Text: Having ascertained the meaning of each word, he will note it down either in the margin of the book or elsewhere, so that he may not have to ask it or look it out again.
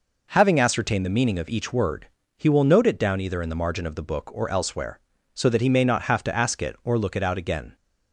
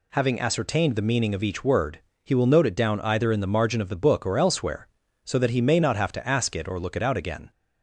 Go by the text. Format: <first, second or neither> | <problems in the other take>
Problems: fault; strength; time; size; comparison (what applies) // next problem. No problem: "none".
neither | none